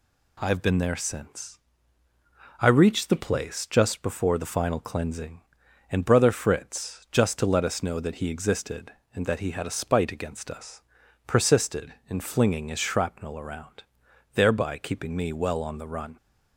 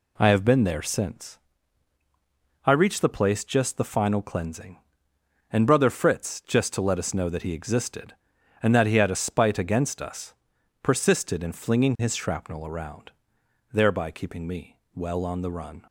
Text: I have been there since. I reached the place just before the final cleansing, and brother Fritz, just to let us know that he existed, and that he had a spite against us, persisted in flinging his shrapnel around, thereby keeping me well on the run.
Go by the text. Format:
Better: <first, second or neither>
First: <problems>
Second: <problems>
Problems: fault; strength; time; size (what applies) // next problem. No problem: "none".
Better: first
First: none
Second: skips "before"; at 3.7 s // pauses between "me" and "well"; slight; at 14.7 s; 0.18 s long